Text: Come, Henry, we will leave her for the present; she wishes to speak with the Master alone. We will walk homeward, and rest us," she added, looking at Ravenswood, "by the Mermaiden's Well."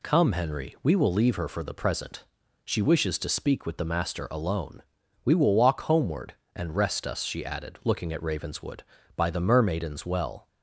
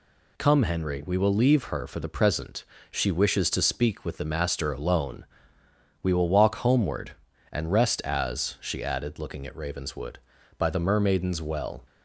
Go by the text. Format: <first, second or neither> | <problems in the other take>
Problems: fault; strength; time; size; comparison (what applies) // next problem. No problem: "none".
first | says "as" for "us"; at 8.0 s